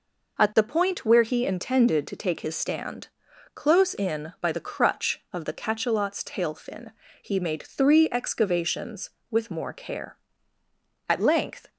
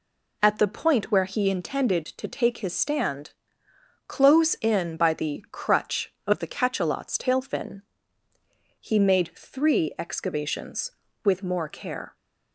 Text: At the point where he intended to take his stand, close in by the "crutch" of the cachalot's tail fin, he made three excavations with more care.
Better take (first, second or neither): second